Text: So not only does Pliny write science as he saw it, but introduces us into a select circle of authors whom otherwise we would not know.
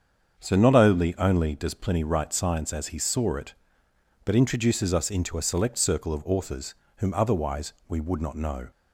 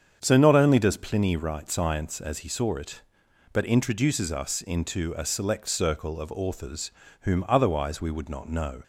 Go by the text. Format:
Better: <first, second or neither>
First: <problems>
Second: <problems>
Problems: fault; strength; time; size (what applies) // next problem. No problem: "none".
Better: second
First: starts louder than the rest; strong; until 1.4 s; 7 dB // says "only" twice; at 1.1 s // pauses between "authors" and "whom"; slight; at 6.7 s; 0.22 s long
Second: starts louder than the rest; strong; until 1.2 s; 7.5 dB // pauses between "authors" and "whom"; slight; at 6.8 s; 0.30 s long